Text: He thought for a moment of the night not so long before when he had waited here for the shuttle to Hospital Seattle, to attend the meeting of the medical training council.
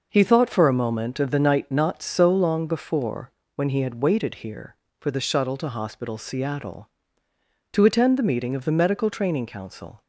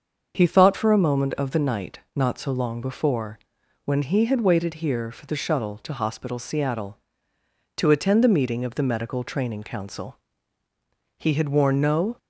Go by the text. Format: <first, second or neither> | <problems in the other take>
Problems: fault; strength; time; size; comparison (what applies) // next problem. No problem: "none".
first | starts louder than the rest; until 1.4 s; 6.5 dB // pauses between "before" and "when"; noticeable; at 3.3 s; 0.48 s long; slight in the first // goes on to say "He had worn no"; noticeable; from 11.1 s on; 1.0 s long